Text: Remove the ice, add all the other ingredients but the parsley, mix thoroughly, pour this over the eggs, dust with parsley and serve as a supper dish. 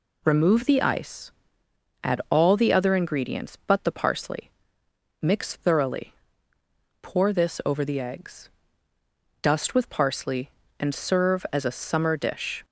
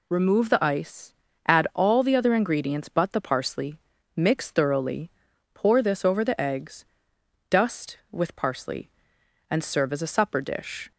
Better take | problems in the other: second | says "summer" for "supper"; at 11.7 s

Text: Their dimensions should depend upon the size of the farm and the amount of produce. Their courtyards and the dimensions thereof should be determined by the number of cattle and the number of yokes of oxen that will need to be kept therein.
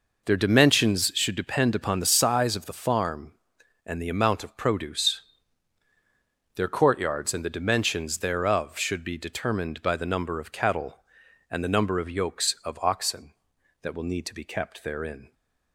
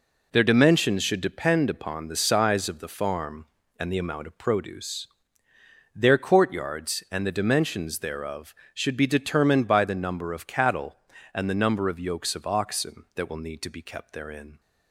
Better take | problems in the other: neither | none

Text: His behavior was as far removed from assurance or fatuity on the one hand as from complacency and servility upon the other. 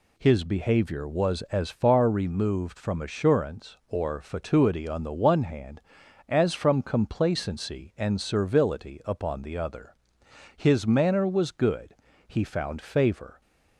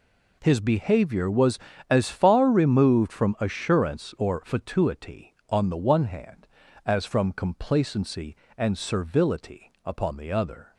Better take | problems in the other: second | goes on to say "His manner was good he found favor"; strong; from 10.5 s on; 2.8 s long

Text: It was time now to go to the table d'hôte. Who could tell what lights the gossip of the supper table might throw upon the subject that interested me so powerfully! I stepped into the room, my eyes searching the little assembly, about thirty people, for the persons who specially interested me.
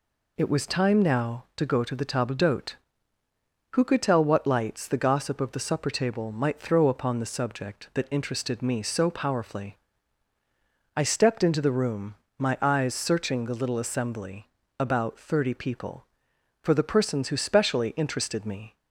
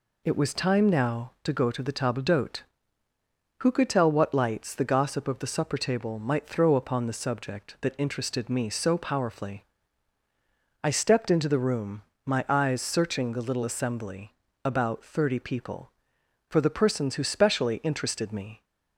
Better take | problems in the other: neither | none

